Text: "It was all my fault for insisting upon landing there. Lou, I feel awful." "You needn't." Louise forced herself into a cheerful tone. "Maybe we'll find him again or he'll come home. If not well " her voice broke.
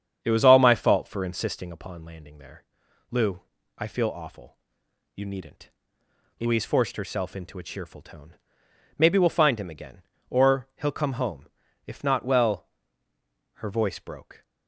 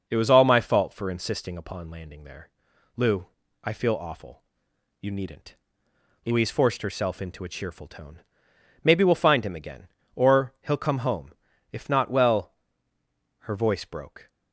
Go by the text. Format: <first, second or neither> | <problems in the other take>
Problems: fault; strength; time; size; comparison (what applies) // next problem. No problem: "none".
second | starts louder than the rest; strong; until 1.7 s; 8 dB